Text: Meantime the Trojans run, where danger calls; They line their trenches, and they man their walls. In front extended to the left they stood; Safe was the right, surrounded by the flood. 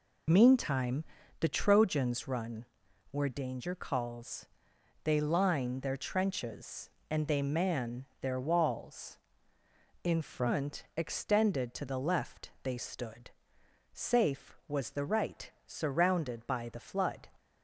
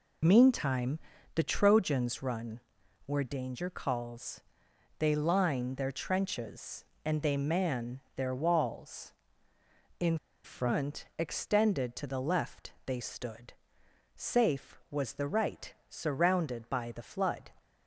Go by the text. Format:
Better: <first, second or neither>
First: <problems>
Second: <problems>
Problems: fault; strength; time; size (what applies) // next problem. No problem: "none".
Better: first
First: pauses between "Meantime" and "the"; slight; at 1.0 s; 0.36 s long // pauses between "man" and "their"; slight; at 8.0 s; 0.16 s long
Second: pauses between "Meantime" and "the"; slight; at 0.9 s; 0.36 s long // pauses between "man" and "their"; slight; at 7.9 s; 0.16 s long // pauses between "In" and "front"; slight; at 10.1 s; 0.28 s long // pauses between "left" and "they"; slight; at 12.7 s; 0.16 s long